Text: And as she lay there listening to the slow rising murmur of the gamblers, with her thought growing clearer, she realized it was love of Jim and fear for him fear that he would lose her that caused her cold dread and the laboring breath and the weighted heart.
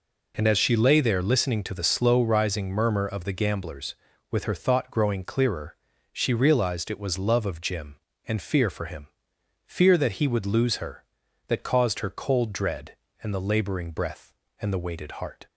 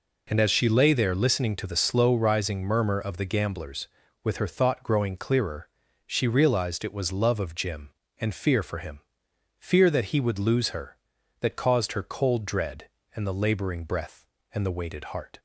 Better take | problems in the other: neither | pauses between "him" and "fear"; noticeable; the same in both

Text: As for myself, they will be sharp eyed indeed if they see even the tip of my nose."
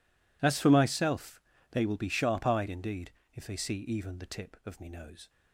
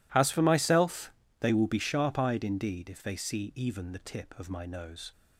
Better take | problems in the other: second | pauses between "indeed" and "if"; slight; at 3.1 s; 0.22 s long // says "me" for "my"; at 4.7 s

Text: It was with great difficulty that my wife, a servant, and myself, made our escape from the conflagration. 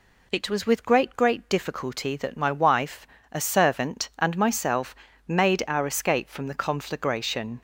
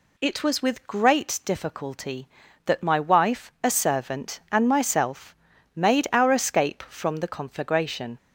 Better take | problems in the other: second | says "great" twice; at 1.1 s

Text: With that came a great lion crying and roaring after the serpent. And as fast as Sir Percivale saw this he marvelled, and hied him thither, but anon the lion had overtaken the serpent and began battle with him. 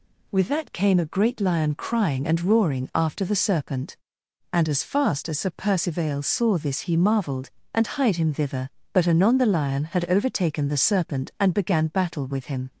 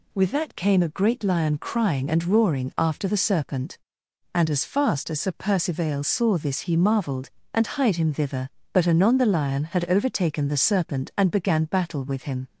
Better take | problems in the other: neither | none

